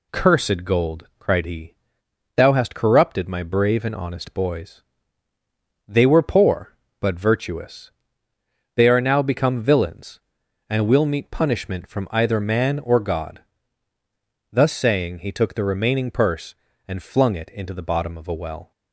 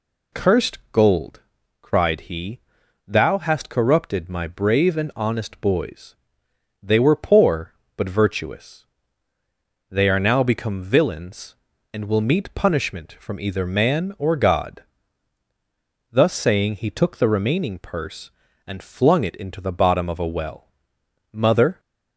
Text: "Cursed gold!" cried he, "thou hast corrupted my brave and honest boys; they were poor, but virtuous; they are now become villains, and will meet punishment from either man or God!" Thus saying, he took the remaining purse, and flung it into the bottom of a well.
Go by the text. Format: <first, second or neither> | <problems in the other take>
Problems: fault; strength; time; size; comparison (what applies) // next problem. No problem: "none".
first | goes on to say "Mother"; slight; from 21.3 s on; 0.48 s long